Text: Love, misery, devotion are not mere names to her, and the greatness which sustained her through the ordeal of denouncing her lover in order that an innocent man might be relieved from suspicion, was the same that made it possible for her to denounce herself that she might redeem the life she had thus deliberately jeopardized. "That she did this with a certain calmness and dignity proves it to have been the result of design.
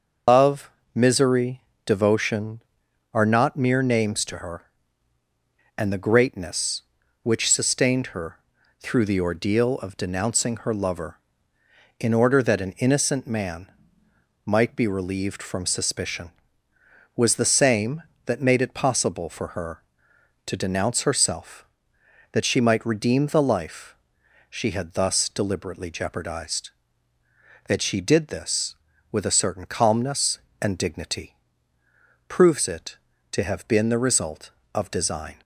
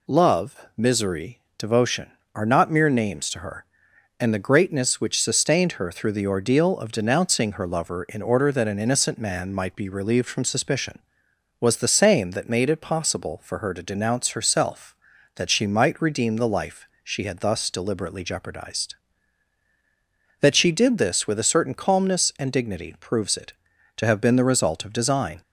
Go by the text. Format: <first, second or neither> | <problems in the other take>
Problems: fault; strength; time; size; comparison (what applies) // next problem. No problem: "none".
second | loses the start of "Love"; at 0.2 s; 130 ms // starts louder than the rest; until 1.5 s; 6.5 dB // pauses between "her" and "through"; at 8.3 s; 0.40 s long // pauses between "man" and "might"; noticeable; at 13.6 s; 0.78 s long // pauses between "life" and "she"; noticeable; at 23.9 s; 0.54 s long; slight in the second // pauses between "dignity" and "proves"; noticeable; at 31.3 s; 0.92 s long